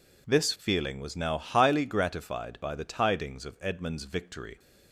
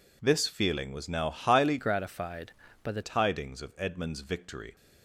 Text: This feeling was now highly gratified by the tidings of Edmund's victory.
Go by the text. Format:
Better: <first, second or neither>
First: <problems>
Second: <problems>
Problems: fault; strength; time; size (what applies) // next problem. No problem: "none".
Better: first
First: none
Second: changes voice from "gratified" to "the"; from 1.7 to 3.0 s; 1.3 s long